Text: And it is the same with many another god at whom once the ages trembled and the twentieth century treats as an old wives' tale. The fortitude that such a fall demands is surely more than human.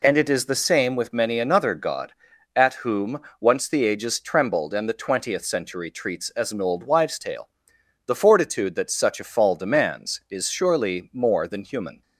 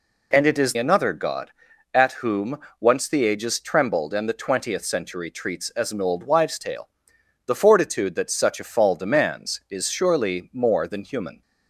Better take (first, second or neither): first